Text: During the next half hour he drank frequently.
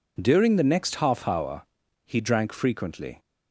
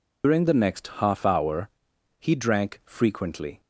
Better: first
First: pauses between "hour" and "he"; at 1.6 s; 0.42 s long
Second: loses the start of "During"; at 0.2 s; 145 ms // pauses between "hour" and "he"; noticeable; at 1.6 s; 0.50 s long

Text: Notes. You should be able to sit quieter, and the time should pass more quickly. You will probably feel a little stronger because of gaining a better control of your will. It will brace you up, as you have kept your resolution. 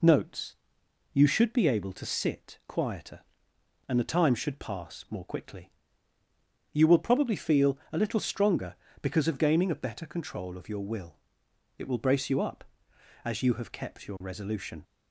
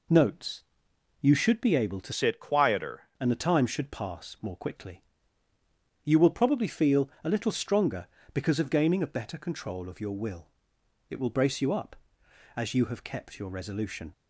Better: first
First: pauses between "feel" and "a"; slight; at 7.7 s; 0.16 s long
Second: changes voice from "sit" to "quieter"; from 2.1 to 3.0 s; 0.9 s long // pauses between "feel" and "a"; slight; at 7.0 s; 0.16 s long

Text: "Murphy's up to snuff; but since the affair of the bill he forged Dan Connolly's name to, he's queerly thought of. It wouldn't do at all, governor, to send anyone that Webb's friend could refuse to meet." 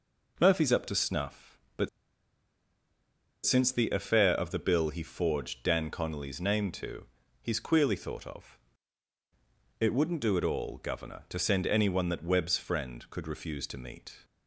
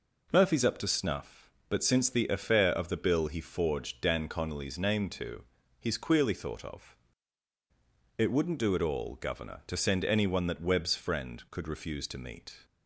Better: second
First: pauses between "but" and "since"; strong; at 1.8 s; 1.5 s long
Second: none

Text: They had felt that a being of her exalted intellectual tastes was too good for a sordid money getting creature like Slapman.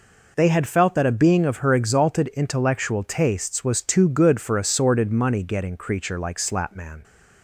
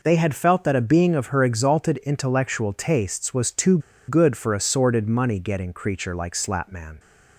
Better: first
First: none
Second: pauses between "too" and "good"; slight; at 3.7 s; 0.29 s long

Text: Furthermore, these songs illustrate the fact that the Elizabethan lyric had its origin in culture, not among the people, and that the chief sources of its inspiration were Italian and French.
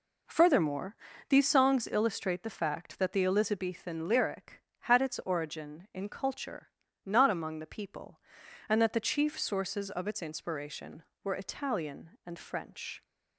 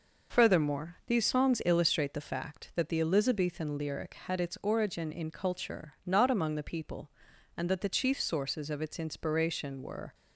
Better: first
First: none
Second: stops before "Italian and French"; at 10.1 s

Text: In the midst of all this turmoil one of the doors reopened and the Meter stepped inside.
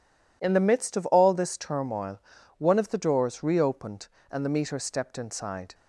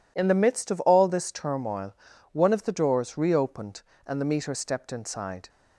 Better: neither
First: pauses between "turmoil" and "one"; at 2.2 s; 0.38 s long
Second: pauses between "turmoil" and "one"; at 1.9 s; 0.38 s long

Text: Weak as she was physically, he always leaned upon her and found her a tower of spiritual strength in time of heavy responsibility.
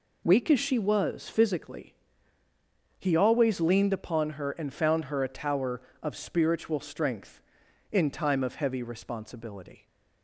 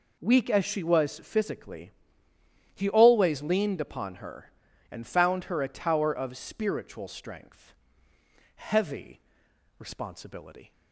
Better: first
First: none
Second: skips "in time of"; at 8.1 s // pauses between "heavy" and "responsibility"; noticeable; at 9.1 s; 0.58 s long

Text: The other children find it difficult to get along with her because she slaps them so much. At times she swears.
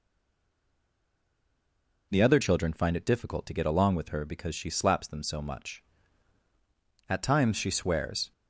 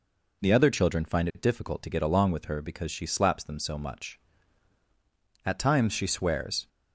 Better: second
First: stays silent before the first word; noticeable; until 2.1 s; 2.1 s long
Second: none

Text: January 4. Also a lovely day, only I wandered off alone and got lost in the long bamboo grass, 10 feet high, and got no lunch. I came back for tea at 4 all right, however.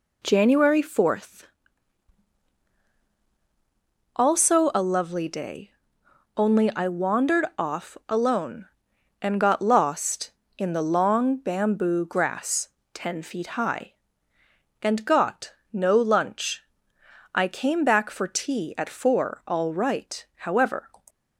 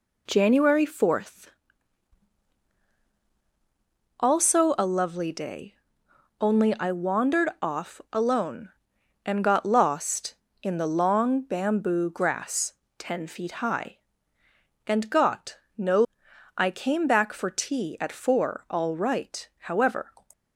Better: first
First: pauses between "got" and "no"; slight; at 15.5 s; 0.18 s long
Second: pauses between "got" and "no"; slight; at 15.5 s; 0.18 s long // skips "lunch"; at 16.2 s

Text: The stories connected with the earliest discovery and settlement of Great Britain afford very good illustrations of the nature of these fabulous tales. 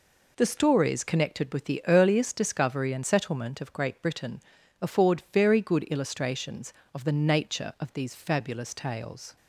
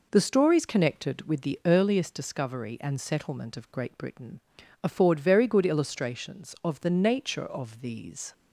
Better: first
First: pauses between "Britain" and "afford"; at 4.3 s; 0.40 s long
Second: pauses between "Britain" and "afford"; at 4.4 s; 0.42 s long // stops before "fabulous tales"; at 8.3 s

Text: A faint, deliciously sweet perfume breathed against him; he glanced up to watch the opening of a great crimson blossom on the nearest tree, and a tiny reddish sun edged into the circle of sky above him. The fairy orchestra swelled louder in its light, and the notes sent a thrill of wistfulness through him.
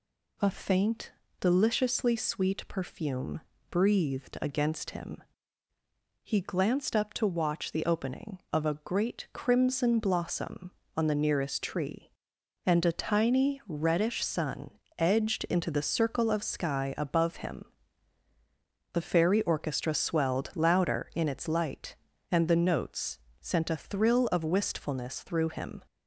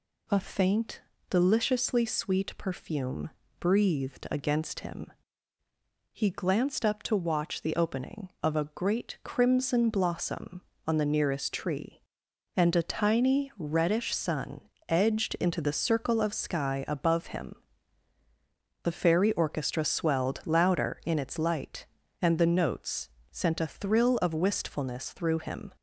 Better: neither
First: pauses between "perfume" and "breathed"; slight; at 3.3 s; 0.32 s long // pauses between "sun" and "edged"; slight; at 14.7 s; 0.24 s long // pauses between "notes" and "sent"; slight; at 23.1 s; 0.24 s long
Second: pauses between "perfume" and "breathed"; slight; at 3.2 s; 0.32 s long // pauses between "sun" and "edged"; slight; at 14.6 s; 0.24 s long // pauses between "notes" and "sent"; slight; at 23.0 s; 0.24 s long

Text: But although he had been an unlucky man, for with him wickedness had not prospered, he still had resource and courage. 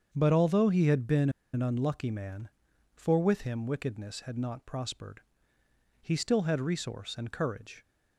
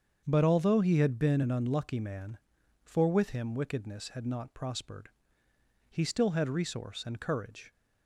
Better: second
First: starts louder than the rest; strong; until 1.1 s; 7 dB // pauses between "been" and "an"; slight; at 1.2 s; 0.24 s long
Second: starts louder than the rest; strong; until 1.2 s; 7 dB

